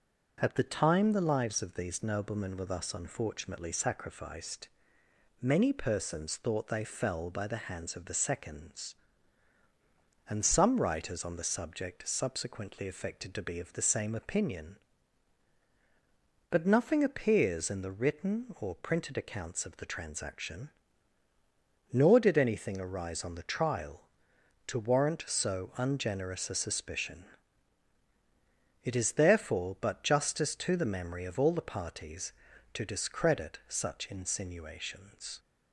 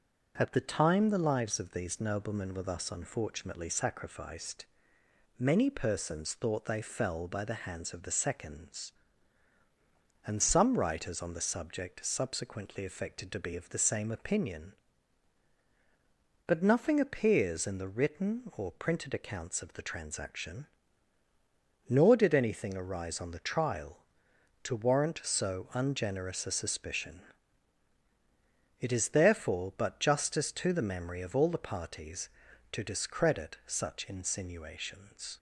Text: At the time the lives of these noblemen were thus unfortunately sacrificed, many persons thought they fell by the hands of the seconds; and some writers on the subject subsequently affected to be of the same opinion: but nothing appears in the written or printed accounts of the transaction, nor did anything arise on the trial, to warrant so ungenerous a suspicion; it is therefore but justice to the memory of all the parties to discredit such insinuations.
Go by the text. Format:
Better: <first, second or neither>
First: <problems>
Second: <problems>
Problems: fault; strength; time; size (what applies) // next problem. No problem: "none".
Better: neither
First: starts louder than the rest; until 1.4 s; 6.5 dB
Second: starts louder than the rest; until 1.3 s; 6.5 dB